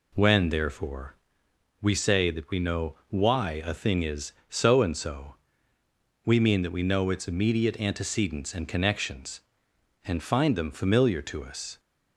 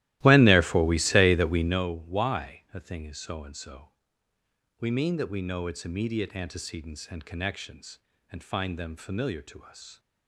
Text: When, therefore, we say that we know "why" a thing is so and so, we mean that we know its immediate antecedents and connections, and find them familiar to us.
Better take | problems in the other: first | starts louder than the rest; strong; until 1.8 s; 15.5 dB

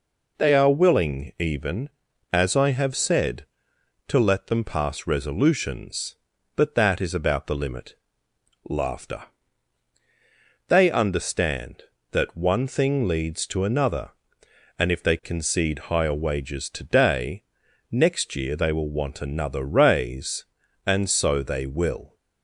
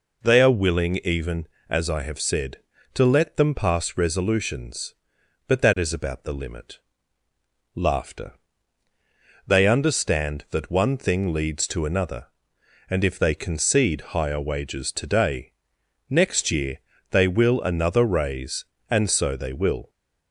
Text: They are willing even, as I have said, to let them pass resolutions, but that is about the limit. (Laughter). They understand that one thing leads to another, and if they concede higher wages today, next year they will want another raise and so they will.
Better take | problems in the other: first | pauses between "year" and "they"; slight; at 16.7 s; 0.32 s long // skips "want"; at 17.6 s

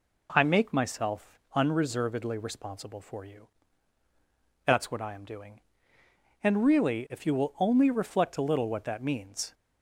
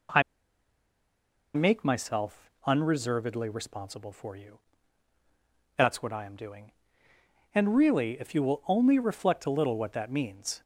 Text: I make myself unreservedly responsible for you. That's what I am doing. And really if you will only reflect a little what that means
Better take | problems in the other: first | pauses between "I" and "make"; strong; at 0.2 s; 1.3 s long // pauses between "myself" and "unreservedly"; slight; at 2.4 s; 0.16 s long; slight in the first

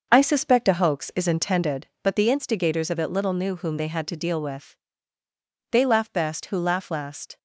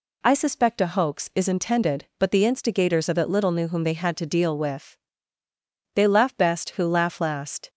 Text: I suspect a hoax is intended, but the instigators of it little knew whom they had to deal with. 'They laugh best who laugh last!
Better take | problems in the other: second | starts louder than the rest; until 1.8 s; 6.5 dB

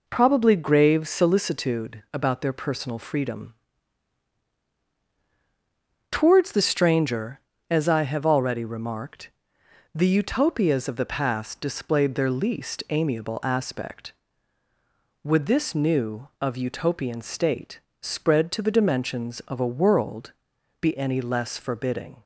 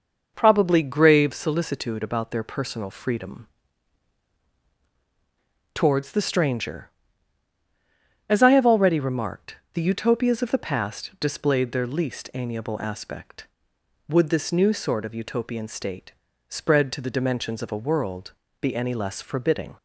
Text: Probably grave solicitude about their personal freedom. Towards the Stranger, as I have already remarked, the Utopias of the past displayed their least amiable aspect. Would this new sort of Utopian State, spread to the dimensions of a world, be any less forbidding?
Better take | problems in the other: second | skips "sort"; at 16.3 s

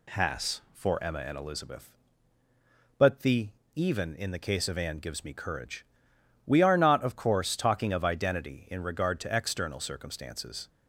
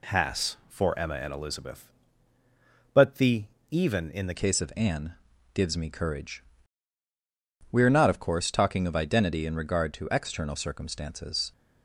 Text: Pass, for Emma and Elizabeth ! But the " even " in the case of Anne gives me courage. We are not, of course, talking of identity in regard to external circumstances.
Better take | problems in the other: first | changes voice at "case"; from 4.3 s on; 7.2 s long // pauses between "Anne" and "gives"; at 5.1 s; 0.40 s long

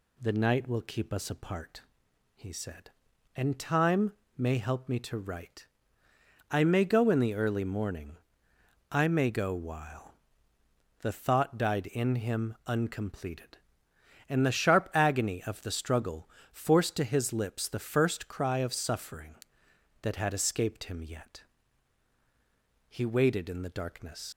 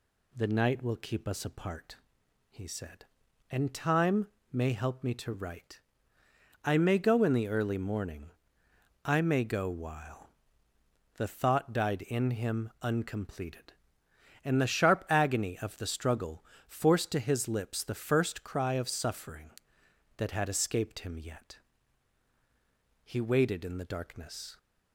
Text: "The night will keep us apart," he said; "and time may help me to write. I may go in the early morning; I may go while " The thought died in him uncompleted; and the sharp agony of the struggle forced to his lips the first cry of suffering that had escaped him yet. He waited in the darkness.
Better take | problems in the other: second | pauses between "time" and "may"; slight; at 4.1 s; 0.22 s long; slight in the second // pauses between "struggle" and "forced"; slight; at 16.2 s; 0.24 s long; slight in the second // leaves "darkness" unfinished; at 24.3 s; 105 ms

